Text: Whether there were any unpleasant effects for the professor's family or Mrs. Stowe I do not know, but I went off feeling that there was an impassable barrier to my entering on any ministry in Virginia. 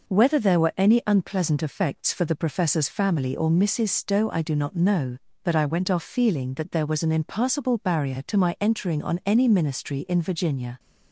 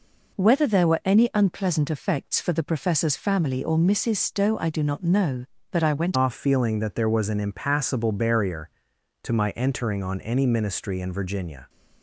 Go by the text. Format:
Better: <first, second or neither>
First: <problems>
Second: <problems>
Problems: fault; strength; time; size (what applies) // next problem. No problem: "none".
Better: first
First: none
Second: changes voice at "off"; from 6.1 s on; 5.5 s long